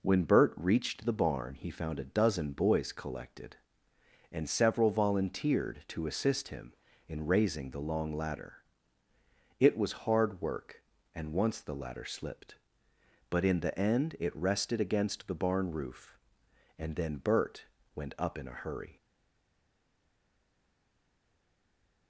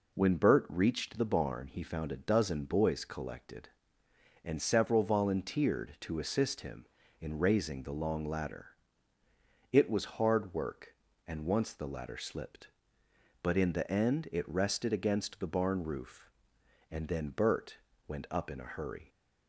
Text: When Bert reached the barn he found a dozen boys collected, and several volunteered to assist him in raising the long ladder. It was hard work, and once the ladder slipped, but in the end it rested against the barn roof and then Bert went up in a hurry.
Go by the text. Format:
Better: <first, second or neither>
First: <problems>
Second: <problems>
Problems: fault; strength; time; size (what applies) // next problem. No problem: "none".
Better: second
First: pauses between "Bert" and "went"; slight; at 17.6 s; 0.28 s long // stays silent after the last word; strong; from 18.9 s on; 3.1 s long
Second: pauses between "Bert" and "went"; slight; at 17.7 s; 0.28 s long